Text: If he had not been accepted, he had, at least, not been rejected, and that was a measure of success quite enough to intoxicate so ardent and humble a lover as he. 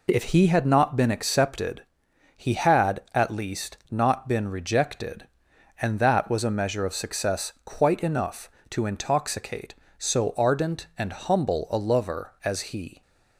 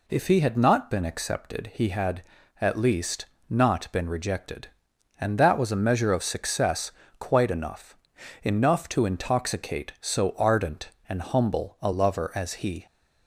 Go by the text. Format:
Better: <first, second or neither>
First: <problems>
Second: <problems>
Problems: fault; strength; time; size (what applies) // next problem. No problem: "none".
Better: first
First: none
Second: pauses between "success" and "quite"; slight; at 6.9 s; 0.28 s long // says "enough" twice; at 8.4 s